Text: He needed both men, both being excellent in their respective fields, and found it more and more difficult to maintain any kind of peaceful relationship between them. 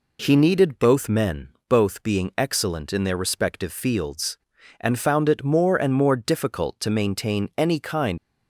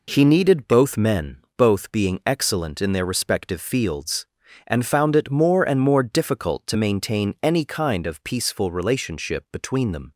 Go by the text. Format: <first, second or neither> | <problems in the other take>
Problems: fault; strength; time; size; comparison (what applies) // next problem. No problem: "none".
second | stops before "of peaceful relationship between them"; at 8.1 s